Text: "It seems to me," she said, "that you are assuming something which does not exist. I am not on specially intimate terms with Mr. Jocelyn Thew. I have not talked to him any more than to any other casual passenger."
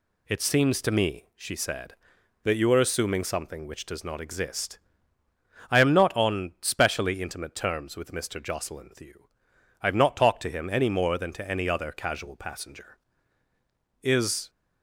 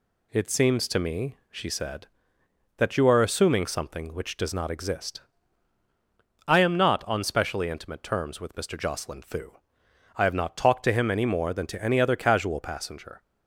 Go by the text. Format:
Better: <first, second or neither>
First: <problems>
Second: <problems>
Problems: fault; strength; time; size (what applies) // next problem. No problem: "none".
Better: second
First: goes on to say "Is"; slight; from 14.0 s on; 0.48 s long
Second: none